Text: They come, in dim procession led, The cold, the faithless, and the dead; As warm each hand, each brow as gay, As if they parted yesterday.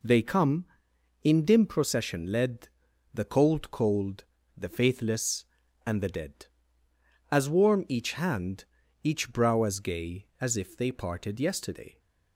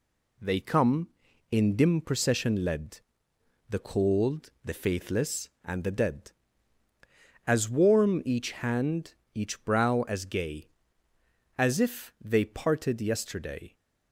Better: second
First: says "cold" twice; at 3.6 s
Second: none

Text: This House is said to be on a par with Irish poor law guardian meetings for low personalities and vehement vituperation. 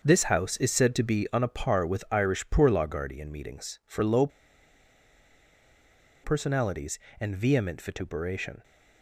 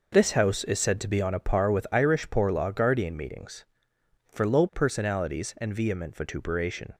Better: second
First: starts louder than the rest; until 1.0 s; 6.5 dB // pauses between "low" and "personalities"; strong; at 4.2 s; 1.9 s long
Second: none

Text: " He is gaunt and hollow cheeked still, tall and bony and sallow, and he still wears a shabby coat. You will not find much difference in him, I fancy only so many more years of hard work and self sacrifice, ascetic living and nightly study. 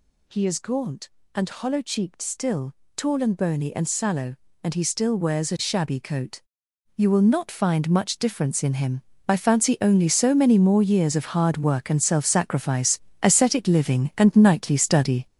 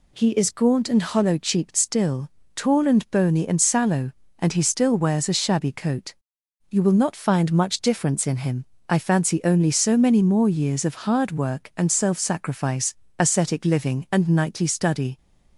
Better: second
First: gets louder; strong; throughout; 8 dB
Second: none

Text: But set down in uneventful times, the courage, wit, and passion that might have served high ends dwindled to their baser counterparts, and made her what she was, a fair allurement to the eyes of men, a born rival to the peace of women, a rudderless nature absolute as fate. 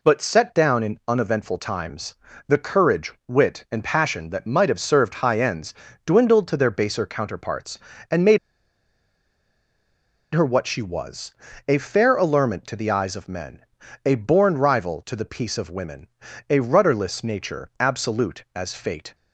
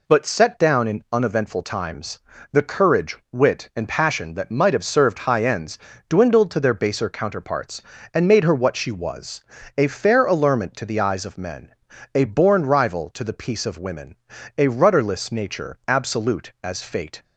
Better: second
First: pauses between "ends" and "dwindled"; slight; at 5.7 s; 0.32 s long // pauses between "made" and "her"; strong; at 8.3 s; 1.9 s long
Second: pauses between "ends" and "dwindled"; slight; at 5.7 s; 0.30 s long

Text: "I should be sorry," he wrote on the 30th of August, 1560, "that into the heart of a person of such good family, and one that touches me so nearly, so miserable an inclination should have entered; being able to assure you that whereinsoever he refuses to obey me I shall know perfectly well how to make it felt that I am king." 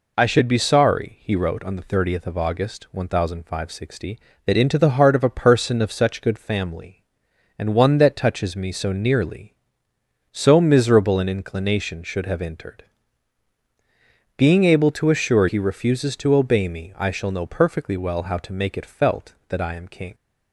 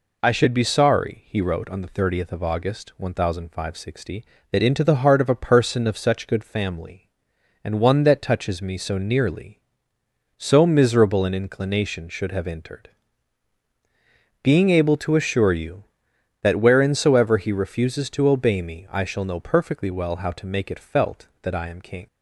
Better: second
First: skips "you that whereinsoever"; at 15.4 s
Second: none

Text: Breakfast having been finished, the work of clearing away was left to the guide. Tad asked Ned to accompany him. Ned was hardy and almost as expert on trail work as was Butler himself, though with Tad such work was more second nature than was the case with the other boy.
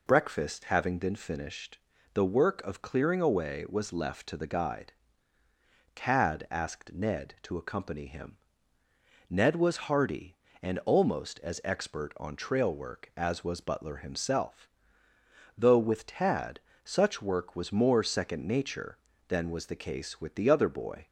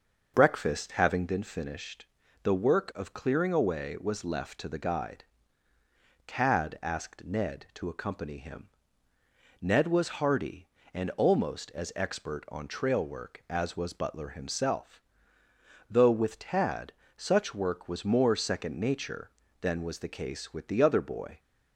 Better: first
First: pauses between "Tad" and "such"; slight; at 16.5 s; 0.26 s long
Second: starts louder than the rest; noticeable; until 1.4 s; 6 dB // pauses between "Tad" and "such"; slight; at 16.9 s; 0.26 s long

